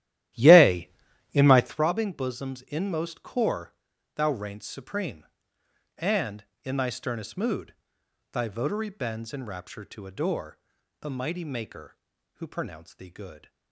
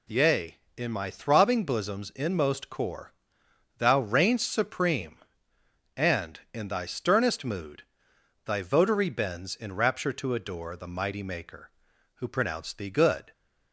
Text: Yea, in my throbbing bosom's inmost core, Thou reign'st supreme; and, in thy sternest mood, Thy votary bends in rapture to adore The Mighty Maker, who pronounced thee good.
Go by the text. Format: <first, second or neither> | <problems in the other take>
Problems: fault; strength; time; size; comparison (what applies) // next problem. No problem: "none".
second | starts louder than the rest; strong; until 1.9 s; 13 dB // pauses between "adore" and "The"; at 10.5 s; 0.42 s long